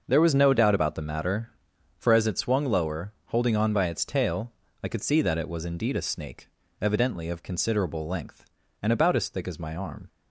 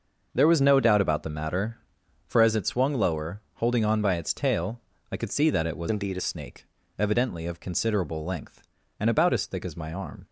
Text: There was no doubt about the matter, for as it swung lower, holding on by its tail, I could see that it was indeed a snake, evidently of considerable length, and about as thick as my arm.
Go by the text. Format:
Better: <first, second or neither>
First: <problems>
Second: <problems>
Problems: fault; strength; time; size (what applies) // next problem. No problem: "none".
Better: first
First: none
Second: starts louder than the rest; noticeable; until 1.3 s; 6 dB // changes voice from "indeed" to "a"; from 5.8 to 6.2 s; 0.4 s long